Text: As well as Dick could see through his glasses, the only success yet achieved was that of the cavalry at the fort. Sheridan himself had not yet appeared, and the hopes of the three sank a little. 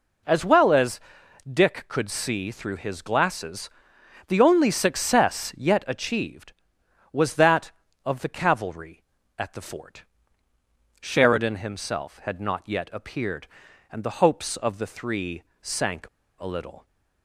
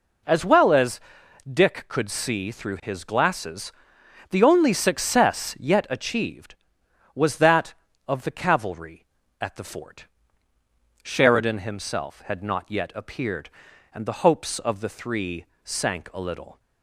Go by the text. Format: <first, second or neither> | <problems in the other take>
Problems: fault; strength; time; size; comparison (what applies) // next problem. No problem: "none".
second | pauses between "as" and "Dick"; noticeable; at 0.9 s; 0.52 s long; noticeable in the second // pauses between "three" and "sank"; slight; at 15.4 s; 0.18 s long; slight in the second // pauses between "sank" and "a"; slight; at 16.0 s; 0.31 s long